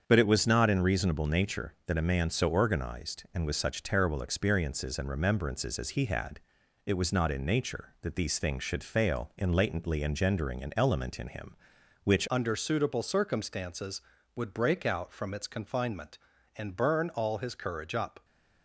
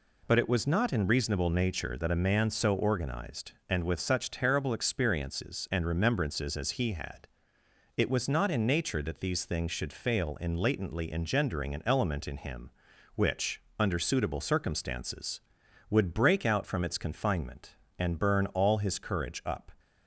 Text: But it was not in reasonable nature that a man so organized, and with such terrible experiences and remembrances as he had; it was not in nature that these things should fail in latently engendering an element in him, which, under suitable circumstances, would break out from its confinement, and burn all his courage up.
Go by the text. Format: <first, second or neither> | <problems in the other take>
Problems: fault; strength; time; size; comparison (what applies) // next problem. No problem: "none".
second | starts louder than the rest; strong; until 1.0 s; 7.5 dB // changes voice at "under"; from 12.3 s on; 5.9 s long